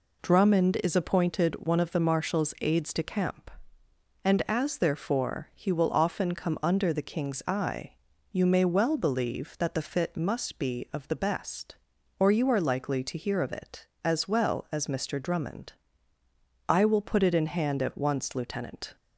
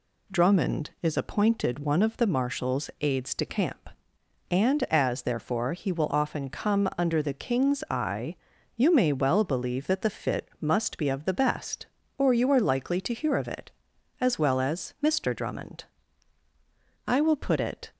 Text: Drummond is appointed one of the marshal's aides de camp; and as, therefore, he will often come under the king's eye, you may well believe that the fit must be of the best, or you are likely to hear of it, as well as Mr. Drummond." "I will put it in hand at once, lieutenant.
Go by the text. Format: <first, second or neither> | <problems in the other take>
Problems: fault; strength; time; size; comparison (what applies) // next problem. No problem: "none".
first | stops before "in hand at once lieutenant"; at 17.9 s